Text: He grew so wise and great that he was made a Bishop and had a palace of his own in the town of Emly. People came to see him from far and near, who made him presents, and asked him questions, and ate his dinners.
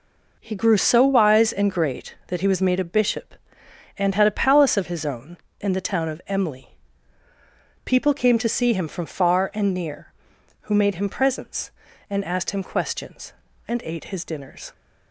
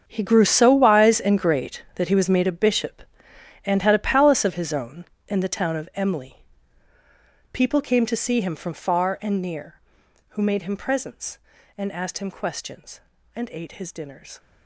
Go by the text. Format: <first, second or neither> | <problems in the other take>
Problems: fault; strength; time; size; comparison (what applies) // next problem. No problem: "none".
first | gets quieter; strong; throughout; 15 dB